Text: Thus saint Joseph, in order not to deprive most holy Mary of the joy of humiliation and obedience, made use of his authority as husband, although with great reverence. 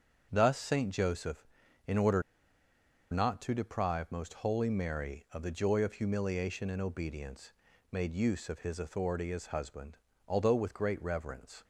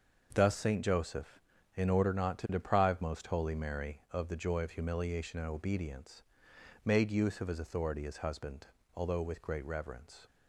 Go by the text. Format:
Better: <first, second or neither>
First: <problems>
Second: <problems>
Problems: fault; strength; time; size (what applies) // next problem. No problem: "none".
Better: second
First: starts louder than the rest; until 1.3 s; 7 dB // pauses between "order" and "not"; noticeable; at 2.2 s; 0.90 s long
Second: starts louder than the rest; until 1.3 s; 6 dB